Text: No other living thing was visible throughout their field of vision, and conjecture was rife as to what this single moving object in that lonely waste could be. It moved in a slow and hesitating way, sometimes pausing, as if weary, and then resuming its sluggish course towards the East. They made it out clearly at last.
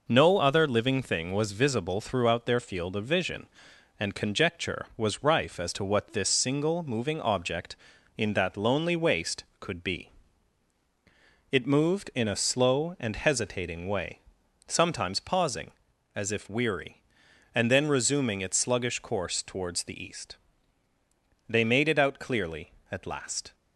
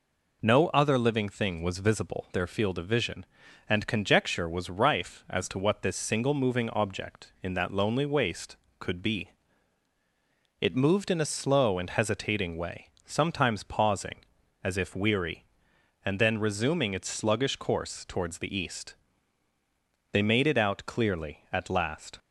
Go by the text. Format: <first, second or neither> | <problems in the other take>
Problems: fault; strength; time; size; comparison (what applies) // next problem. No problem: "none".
first | skips "throughout"; at 2.2 s